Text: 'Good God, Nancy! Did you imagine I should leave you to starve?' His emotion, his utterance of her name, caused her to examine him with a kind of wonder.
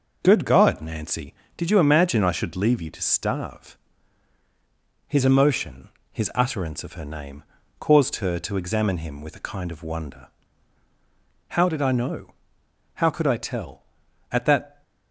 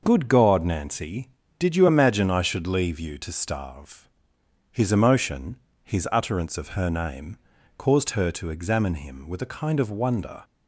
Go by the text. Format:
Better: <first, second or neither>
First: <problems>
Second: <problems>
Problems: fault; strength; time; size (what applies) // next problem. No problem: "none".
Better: second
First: goes on to say "How did I know How could I tell at that"; strong; from 11.5 s on; 3.3 s long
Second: none